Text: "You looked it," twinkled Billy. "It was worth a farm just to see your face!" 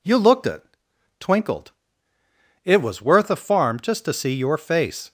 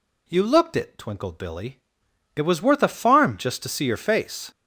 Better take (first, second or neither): second